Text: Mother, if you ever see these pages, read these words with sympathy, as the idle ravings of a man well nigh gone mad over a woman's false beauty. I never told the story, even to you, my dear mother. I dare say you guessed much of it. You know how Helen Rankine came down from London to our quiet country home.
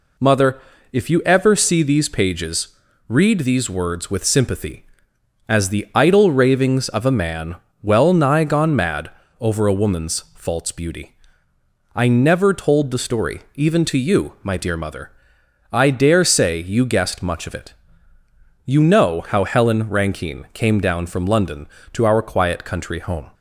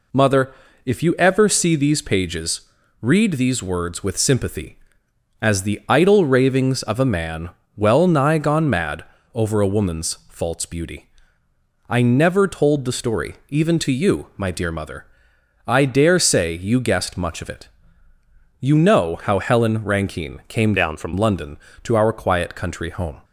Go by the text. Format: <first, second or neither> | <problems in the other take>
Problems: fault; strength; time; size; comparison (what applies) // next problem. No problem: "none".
first | pauses between "man" and "well"; slight; at 7.5 s; 0.26 s long; slight in the first // pauses between "mad" and "over"; slight; at 9.0 s; 0.30 s long; slight in the first // pauses between "woman's" and "false"; slight; at 10.1 s; 0.16 s long; slight in the first // changes voice from "down" to "from"; from 20.7 to 21.1 s; 0.4 s long